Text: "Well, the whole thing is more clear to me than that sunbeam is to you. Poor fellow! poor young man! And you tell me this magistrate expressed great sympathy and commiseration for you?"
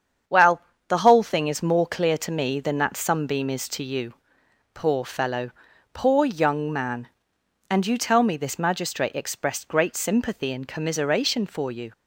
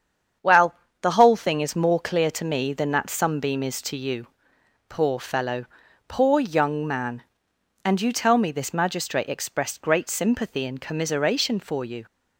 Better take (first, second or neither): neither